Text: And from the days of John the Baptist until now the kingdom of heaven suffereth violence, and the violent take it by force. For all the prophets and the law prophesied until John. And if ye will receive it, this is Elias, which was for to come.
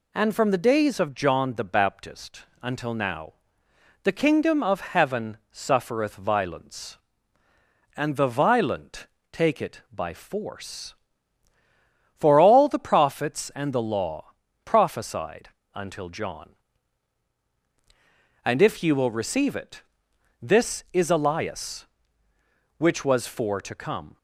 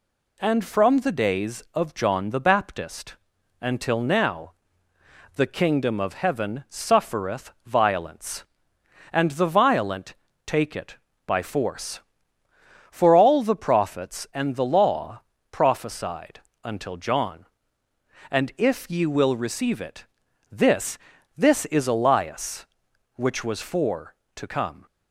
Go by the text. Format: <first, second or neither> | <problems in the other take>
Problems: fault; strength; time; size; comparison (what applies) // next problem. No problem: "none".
first | pauses between "Baptist" and "until"; noticeable; at 3.1 s; 0.46 s long; slight in the first // pauses between "now" and "the"; noticeable; at 4.5 s; 0.82 s long; noticeable in the first // pauses between "suffereth" and "violence"; slight; at 7.4 s; 0.16 s long // pauses between "violent" and "take"; slight; at 10.1 s; 0.32 s long; slight in the first // pauses between "law" and "prophesied"; slight; at 15.2 s; 0.30 s long; slight in the first // pauses between "prophesied" and "until"; slight; at 16.3 s; 0.24 s long; slight in the first // says "this" twice; at 21.3 s